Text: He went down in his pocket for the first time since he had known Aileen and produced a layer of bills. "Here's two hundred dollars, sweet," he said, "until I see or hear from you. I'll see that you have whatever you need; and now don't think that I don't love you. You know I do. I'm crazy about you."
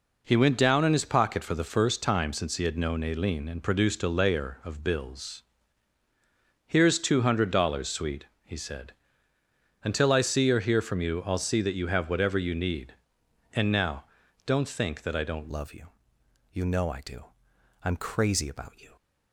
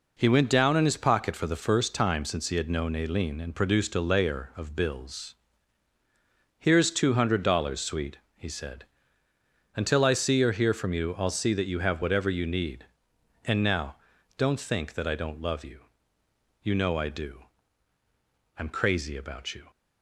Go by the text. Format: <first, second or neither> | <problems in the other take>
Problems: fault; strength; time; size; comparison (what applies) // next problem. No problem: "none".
second | pauses between "now" and "don't"; at 14.0 s; 0.40 s long; also in the second // changes voice at "love"; from 15.4 s on; 3.5 s long